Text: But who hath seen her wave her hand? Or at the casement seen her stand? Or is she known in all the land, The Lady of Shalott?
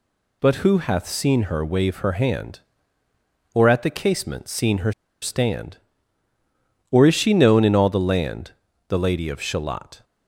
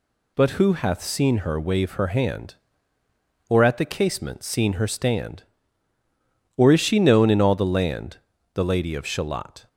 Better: second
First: pauses between "her" and "stand"; slight; at 4.9 s; 0.30 s long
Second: none

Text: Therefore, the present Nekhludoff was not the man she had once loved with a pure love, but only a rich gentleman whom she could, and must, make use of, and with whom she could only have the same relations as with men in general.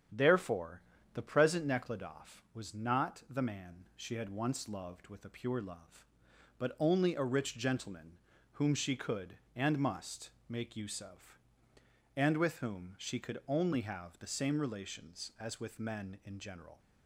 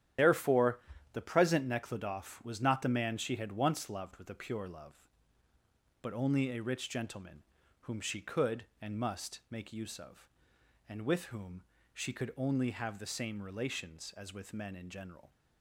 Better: first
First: starts louder than the rest; strong; until 1.4 s; 8.5 dB // pauses between "gentleman" and "whom"; at 8.1 s; 0.40 s long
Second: loses the start of "Therefore"; at 0.1 s; 70 ms // starts louder than the rest; strong; until 1.5 s; 10.5 dB // pauses between "gentleman" and "whom"; at 7.4 s; 0.40 s long // pauses between "whom" and "she"; slight; at 11.6 s; 0.32 s long

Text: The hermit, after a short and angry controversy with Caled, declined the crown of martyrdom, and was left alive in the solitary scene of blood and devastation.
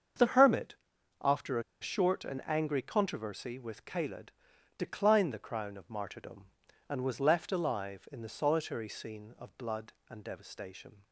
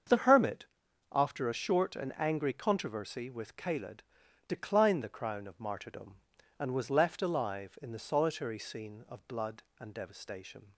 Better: second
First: starts louder than the rest; until 1.8 s; 7 dB // pauses between "a" and "short"; slight; at 1.6 s; 0.18 s long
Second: starts louder than the rest; until 1.5 s; 7 dB

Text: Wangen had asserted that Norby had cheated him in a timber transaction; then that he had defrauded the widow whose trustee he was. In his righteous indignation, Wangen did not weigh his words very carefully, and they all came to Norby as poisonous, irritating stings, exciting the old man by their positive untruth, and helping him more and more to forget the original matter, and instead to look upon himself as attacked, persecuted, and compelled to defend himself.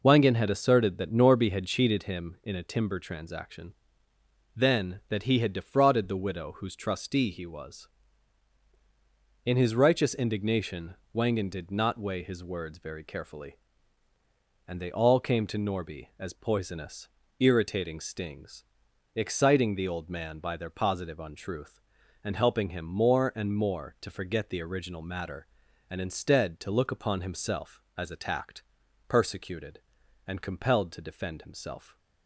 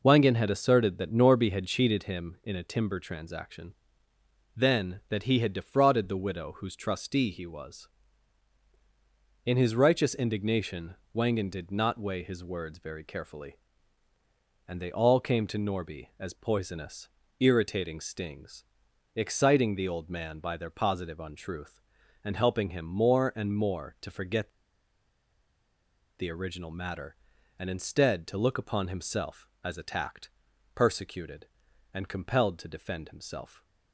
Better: first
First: none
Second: pauses between "forget" and "the"; strong; at 24.4 s; 1.6 s long

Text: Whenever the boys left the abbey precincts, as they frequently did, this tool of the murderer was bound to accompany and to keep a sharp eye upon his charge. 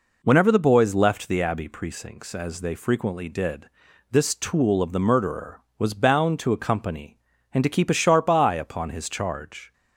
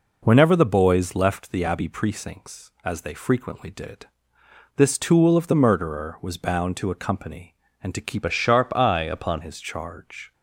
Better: first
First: none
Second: changes voice from "a" to "upon"; from 8.2 to 9.4 s; 1.2 s long

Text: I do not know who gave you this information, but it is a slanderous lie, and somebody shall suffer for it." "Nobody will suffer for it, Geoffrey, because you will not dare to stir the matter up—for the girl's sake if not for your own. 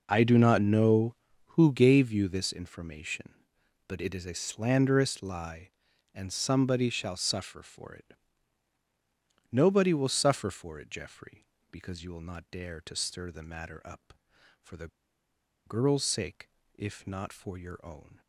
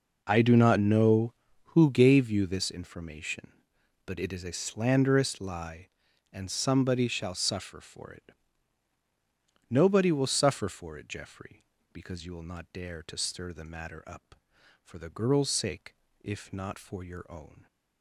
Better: second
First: pauses between "the" and "girl's"; noticeable; at 14.8 s; 0.77 s long // pauses between "sake" and "if"; slight; at 16.4 s; 0.24 s long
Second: pauses between "sake" and "if"; slight; at 15.9 s; 0.24 s long

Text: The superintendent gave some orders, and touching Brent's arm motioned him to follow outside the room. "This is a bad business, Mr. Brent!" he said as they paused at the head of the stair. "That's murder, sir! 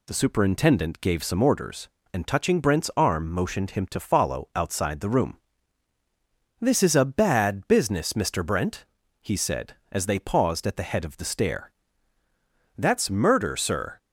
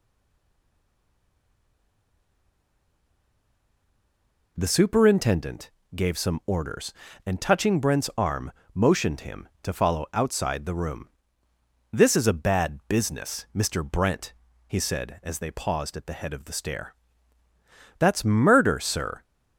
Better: first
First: none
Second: stays silent before the first word; strong; until 4.5 s; 4.5 s long // pauses between "superintendent" and "gave"; slight; at 5.7 s; 0.24 s long // pauses between "arm" and "motioned"; slight; at 8.5 s; 0.20 s long

